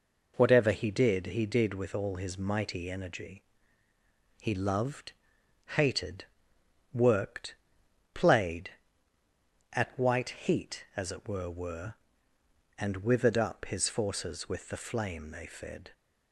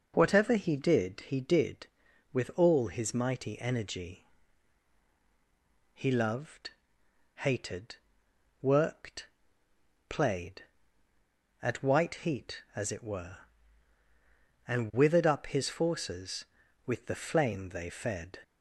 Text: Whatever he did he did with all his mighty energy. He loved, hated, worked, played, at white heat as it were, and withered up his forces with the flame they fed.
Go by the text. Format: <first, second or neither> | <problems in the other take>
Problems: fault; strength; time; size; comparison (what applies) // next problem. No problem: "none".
second | says "were" twice; at 11.4 s